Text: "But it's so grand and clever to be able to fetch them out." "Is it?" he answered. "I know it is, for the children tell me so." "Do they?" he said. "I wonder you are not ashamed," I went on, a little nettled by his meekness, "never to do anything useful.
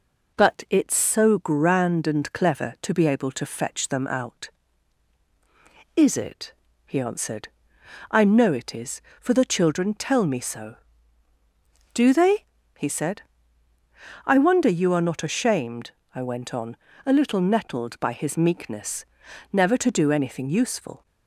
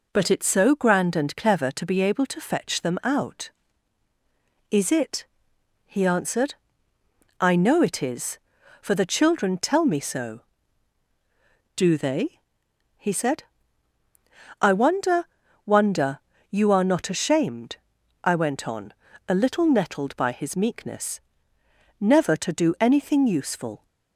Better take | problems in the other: first | says "wonder" twice; at 15.6 s

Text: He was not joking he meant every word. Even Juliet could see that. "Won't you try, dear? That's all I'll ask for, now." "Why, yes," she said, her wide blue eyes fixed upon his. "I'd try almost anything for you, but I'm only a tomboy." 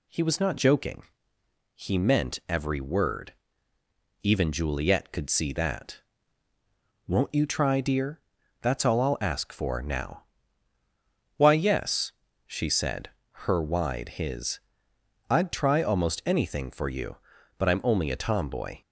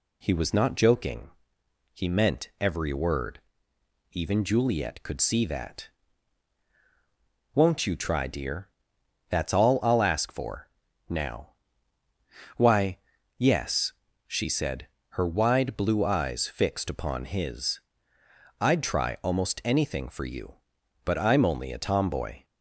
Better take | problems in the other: second | pauses between "joking" and "he"; noticeable; at 1.0 s; 0.78 s long; noticeable in the second // skips "blue eyes fixed upon"; at 14.1 s

